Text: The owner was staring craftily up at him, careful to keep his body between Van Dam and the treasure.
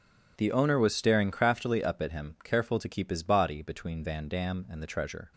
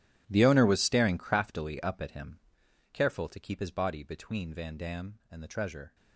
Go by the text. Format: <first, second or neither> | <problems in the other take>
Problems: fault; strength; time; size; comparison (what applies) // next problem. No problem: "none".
first | gets quieter; strong; throughout; 17 dB